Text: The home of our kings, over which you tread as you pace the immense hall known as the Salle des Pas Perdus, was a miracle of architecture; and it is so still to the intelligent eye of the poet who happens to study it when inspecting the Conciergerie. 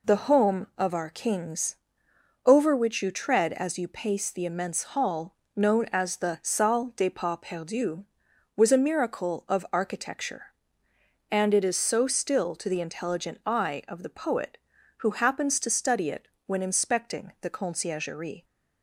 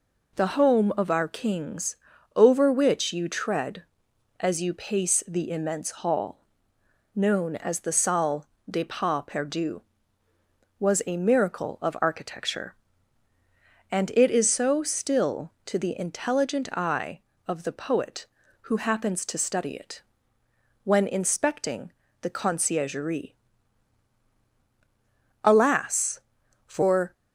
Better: first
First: pauses between "hall" and "known"; slight; at 5.3 s; 0.22 s long // pauses between "it" and "when"; slight; at 16.2 s; 0.18 s long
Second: pauses between "hall" and "known"; noticeable; at 6.3 s; 0.76 s long // pauses between "Salle" and "des"; slight; at 8.4 s; 0.20 s long // pauses between "it" and "when"; noticeable; at 20.0 s; 0.82 s long // pauses between "inspecting" and "the"; slight; at 21.9 s; 0.30 s long // goes on to say "Alas for"; strong; from 25.4 s on; 1.7 s long

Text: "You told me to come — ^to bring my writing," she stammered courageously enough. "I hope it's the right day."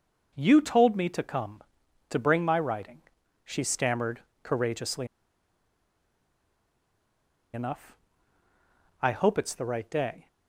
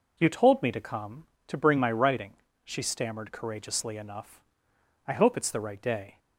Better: second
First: pauses between "stammered" and "courageously"; slight; at 4.2 s; 0.22 s long // pauses between "courageously" and "enough"; strong; at 5.0 s; 2.4 s long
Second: none

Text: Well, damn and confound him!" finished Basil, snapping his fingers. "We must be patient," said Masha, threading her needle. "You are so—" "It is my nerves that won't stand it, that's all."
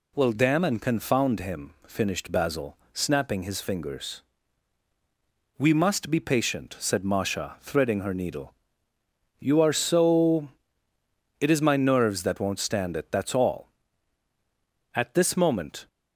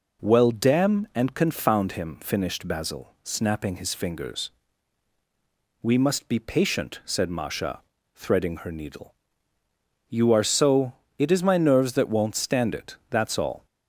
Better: second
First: goes on to say "At this moment"; noticeable; from 14.9 s on; 0.94 s long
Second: none

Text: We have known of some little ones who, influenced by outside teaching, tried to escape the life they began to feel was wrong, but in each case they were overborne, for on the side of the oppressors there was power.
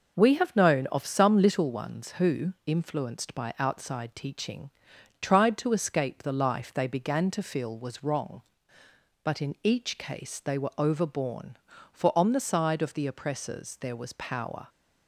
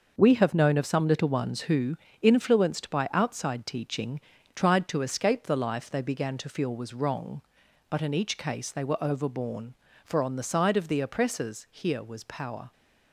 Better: first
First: none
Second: starts louder than the rest; noticeable; until 1.1 s; 6 dB // says "here" for "there"; at 11.6 s

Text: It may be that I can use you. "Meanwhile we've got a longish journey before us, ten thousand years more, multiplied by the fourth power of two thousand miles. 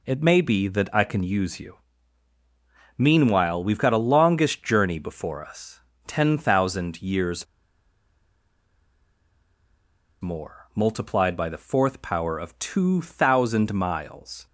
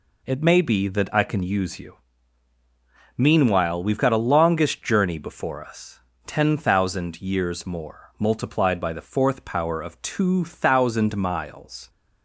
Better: second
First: pauses between "years" and "more"; strong; at 7.4 s; 2.7 s long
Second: none

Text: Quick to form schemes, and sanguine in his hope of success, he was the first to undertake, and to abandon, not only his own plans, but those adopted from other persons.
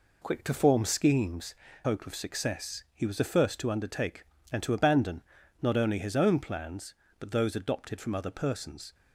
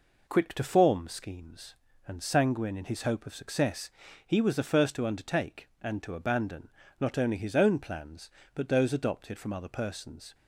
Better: second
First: skips "and sanguine in his"; at 1.6 s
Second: none

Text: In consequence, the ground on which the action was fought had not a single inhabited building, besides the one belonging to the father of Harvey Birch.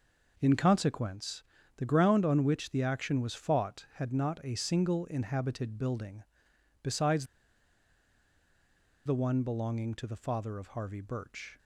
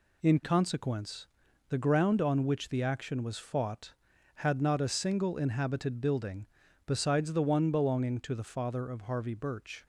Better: second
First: pauses between "besides" and "the"; strong; at 7.2 s; 1.8 s long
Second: none

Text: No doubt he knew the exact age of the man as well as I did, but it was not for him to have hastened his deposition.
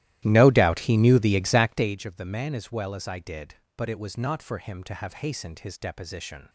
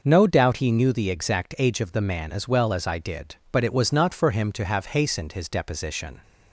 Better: second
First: starts louder than the rest; strong; until 2.0 s; 14.5 dB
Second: none

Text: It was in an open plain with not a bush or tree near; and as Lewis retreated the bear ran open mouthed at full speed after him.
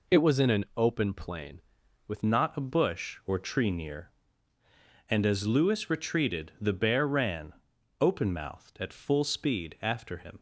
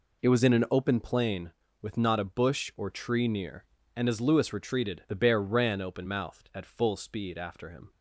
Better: second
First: changes voice at "not"; from 2.2 s on; 8.1 s long // pauses between "ran" and "open"; noticeable; at 7.5 s; 0.46 s long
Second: none

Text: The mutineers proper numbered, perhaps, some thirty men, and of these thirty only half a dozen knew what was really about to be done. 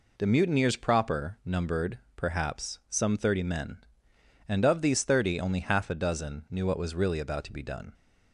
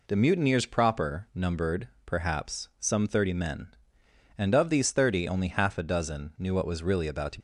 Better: first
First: none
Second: stops before "be done"; at 7.3 s

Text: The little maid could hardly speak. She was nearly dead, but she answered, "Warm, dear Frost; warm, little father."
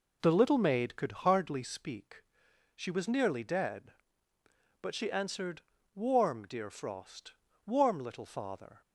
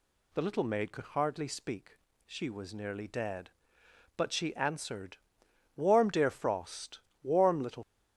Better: first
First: none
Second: stops before "father"; at 7.8 s

